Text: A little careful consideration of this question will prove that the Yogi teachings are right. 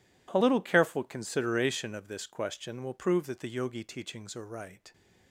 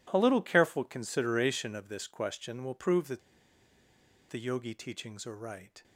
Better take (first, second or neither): first